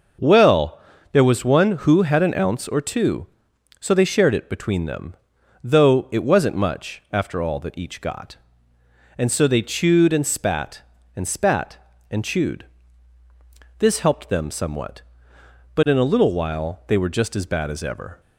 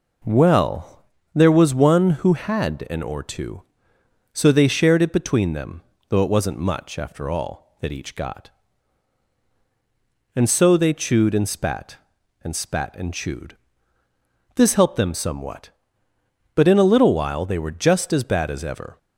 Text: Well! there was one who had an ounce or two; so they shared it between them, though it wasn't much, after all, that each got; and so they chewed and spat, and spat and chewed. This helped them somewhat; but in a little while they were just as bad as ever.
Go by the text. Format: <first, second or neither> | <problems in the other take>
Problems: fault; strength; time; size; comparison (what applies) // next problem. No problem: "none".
first | skips "ounce"; at 3.0 s